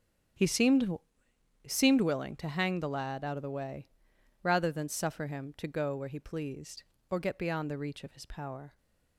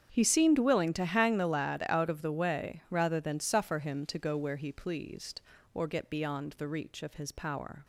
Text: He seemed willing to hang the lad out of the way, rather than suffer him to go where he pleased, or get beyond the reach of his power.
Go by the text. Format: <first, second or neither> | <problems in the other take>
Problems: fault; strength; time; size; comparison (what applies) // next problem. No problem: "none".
second | starts louder than the rest; strong; until 2.1 s; 9 dB; strong in the second // says "seemed" twice; at 1.6 s